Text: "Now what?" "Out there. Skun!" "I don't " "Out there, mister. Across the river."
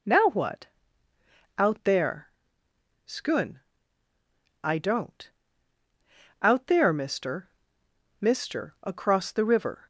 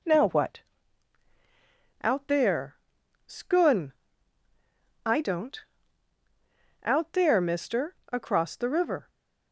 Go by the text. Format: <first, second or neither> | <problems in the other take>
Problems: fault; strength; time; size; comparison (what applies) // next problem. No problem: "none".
second | says "mister" twice; at 8.2 s